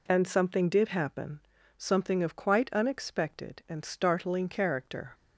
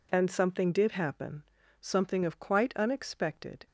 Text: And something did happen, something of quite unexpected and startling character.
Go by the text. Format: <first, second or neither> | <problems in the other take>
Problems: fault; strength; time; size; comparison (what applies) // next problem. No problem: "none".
first | stops before "and startling character"; at 3.6 s